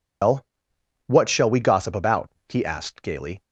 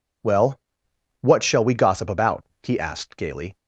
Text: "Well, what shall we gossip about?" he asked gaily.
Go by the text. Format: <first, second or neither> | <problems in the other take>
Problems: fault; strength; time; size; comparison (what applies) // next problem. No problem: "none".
second | loses the start of "Well"; at 0.2 s; 120 ms